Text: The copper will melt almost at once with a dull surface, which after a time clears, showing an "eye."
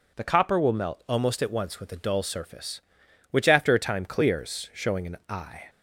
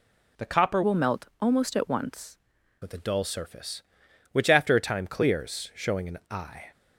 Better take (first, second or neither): first